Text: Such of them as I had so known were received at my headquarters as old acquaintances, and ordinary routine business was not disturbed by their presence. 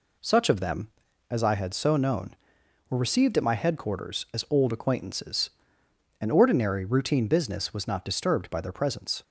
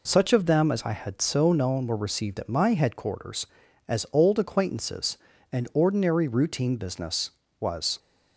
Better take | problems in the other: first | stops before "not disturbed by their presence"; at 7.9 s

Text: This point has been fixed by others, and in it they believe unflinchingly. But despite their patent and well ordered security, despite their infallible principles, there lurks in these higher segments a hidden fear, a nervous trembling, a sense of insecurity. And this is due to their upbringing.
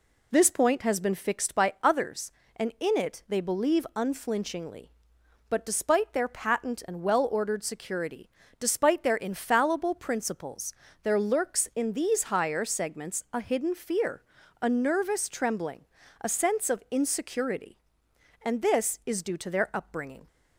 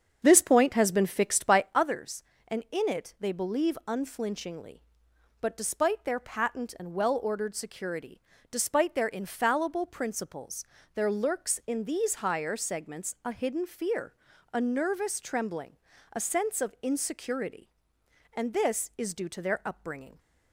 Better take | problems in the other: first | starts louder than the rest; strong; until 1.8 s; 7 dB

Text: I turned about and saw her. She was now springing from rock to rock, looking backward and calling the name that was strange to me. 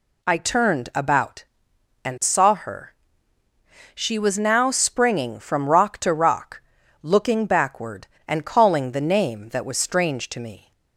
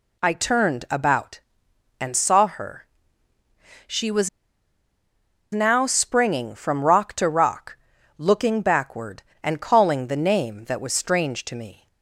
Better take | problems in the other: first | pauses between "was" and "now"; strong; at 4.2 s; 1.2 s long

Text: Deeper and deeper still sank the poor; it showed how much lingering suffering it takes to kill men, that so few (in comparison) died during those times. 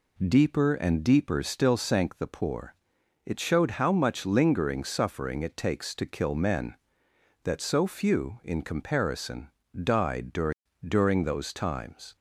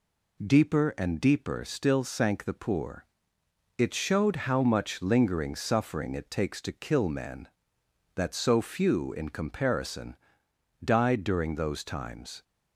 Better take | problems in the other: second | says "during" twice; at 10.8 s

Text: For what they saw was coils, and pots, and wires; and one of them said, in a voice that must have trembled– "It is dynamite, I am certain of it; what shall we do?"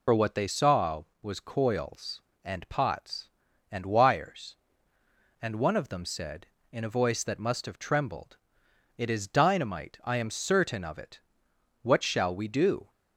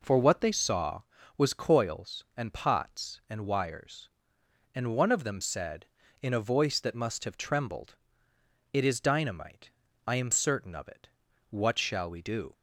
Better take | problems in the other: second | loses the start of "For"; at 0.0 s; 60 ms

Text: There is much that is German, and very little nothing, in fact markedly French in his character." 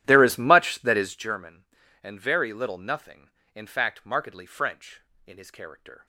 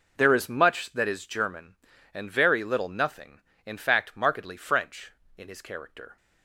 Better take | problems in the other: second | starts louder than the rest; strong; until 1.3 s; 12.5 dB

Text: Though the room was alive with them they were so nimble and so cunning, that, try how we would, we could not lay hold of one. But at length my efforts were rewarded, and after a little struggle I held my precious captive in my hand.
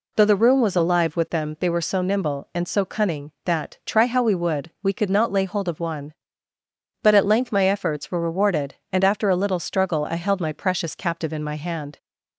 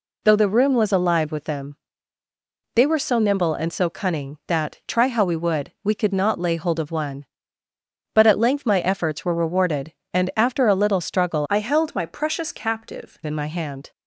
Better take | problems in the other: first | pauses between "them" and "they"; at 1.7 s; 1.0 s long // changes voice from "I" to "captive"; from 11.4 to 13.1 s; 1.7 s long

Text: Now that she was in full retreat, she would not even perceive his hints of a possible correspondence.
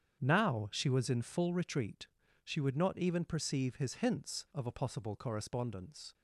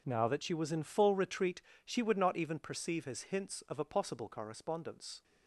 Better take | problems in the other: second | starts louder than the rest; strong; until 1.2 s; 8 dB // skips "that"; at 0.6 s

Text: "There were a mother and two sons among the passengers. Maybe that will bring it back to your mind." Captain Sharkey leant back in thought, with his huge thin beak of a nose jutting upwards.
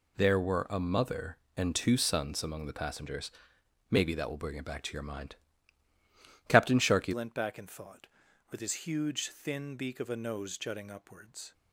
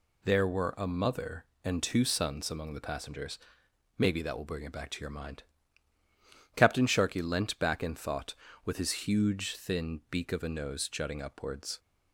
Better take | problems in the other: second | changes voice at "leant"; from 7.1 s on; 4.4 s long

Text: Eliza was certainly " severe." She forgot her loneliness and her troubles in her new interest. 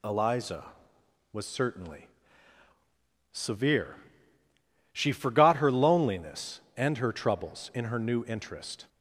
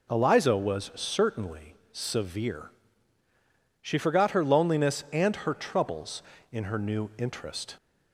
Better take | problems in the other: neither | none

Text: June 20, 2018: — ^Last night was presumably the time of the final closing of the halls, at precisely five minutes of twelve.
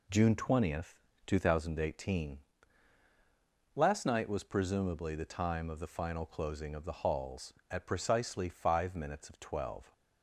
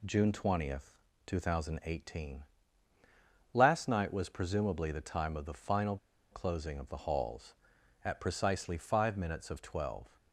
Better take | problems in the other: first | pauses between "final" and "closing"; slight; at 5.9 s; 0.35 s long

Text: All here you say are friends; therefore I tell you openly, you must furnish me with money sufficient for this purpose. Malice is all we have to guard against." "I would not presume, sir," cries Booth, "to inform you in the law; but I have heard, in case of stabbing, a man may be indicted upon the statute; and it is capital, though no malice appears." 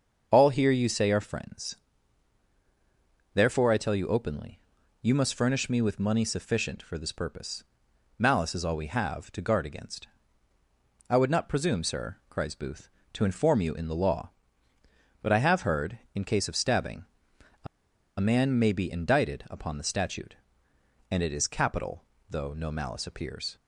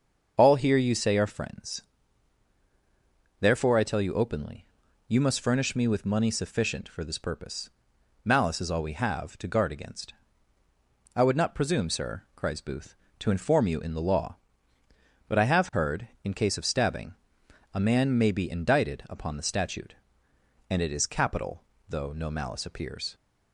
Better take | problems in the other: second | starts louder than the rest; until 1.3 s; 6.5 dB; also in the second // pauses between "a" and "man"; noticeable; at 17.6 s; 0.52 s long

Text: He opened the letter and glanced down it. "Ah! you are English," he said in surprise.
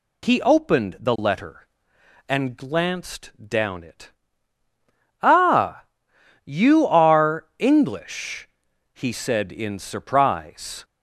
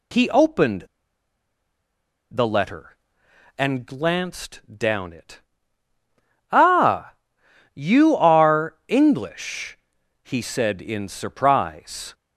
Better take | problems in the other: first | pauses between "opened" and "the"; strong; at 0.8 s; 1.4 s long // pauses between "glanced" and "down"; slight; at 4.5 s; 0.18 s long; slight in the first

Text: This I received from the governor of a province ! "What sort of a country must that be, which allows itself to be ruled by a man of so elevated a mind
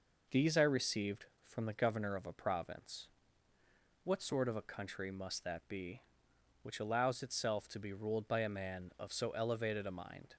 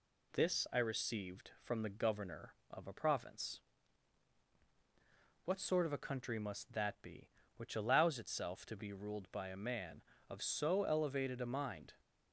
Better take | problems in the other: second | says "These" for "This"; at 0.2 s

